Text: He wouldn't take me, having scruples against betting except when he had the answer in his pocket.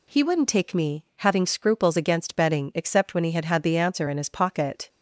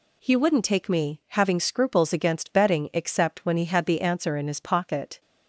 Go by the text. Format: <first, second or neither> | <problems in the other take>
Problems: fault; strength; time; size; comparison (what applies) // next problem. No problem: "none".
second | says "had" twice; at 3.4 s